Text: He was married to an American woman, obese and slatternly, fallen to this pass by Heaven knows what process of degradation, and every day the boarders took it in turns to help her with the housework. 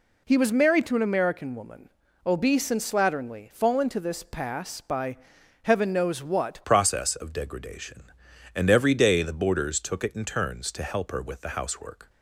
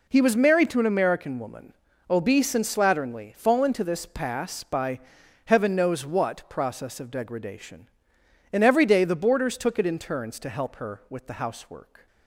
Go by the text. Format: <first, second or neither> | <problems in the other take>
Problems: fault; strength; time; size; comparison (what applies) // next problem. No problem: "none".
second | pauses between "by" and "Heaven"; noticeable; at 5.1 s; 0.46 s long; noticeable in the second // changes voice at "process"; from 6.6 s on; 5.4 s long